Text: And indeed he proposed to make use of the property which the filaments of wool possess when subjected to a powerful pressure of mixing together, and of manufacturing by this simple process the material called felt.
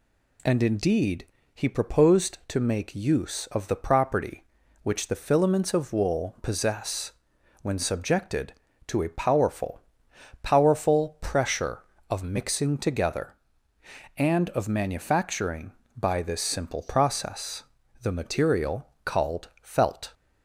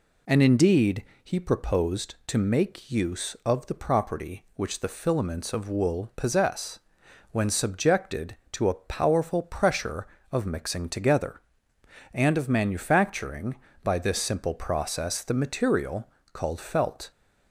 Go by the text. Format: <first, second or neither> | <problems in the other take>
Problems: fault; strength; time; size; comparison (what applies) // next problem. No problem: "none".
second | pauses between "indeed" and "he"; slight; at 1.2 s; 0.28 s long; slight in the second // pauses between "possess" and "when"; noticeable; at 7.1 s; 0.52 s long; noticeable in the second // says "powerful" twice; at 10.4 s // pauses between "process" and "the"; at 17.6 s; 0.38 s long // pauses between "material" and "called"; slight; at 18.8 s; 0.16 s long; slight in the second